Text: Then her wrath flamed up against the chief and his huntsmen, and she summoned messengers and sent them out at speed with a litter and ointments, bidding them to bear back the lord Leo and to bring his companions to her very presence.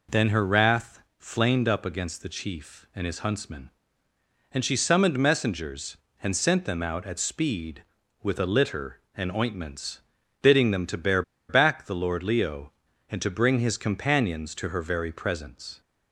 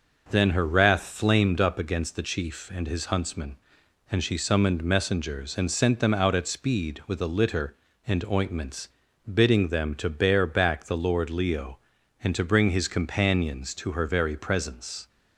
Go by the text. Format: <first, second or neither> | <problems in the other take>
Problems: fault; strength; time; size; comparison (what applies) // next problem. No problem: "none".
second | pauses between "wrath" and "flamed"; slight; at 0.9 s; 0.18 s long // pauses between "bear" and "back"; slight; at 11.2 s; 0.27 s long